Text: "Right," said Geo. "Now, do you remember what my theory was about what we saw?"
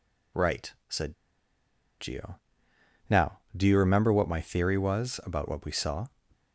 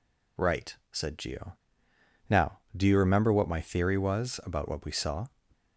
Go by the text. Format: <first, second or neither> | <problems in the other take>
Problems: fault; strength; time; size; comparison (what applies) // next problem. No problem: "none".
second | pauses between "said" and "Geo"; noticeable; at 1.1 s; 0.86 s long